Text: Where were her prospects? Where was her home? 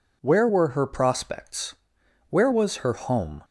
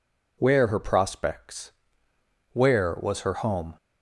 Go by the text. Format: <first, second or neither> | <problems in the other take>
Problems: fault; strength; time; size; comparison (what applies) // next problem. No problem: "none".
first | skips "were"; at 0.6 s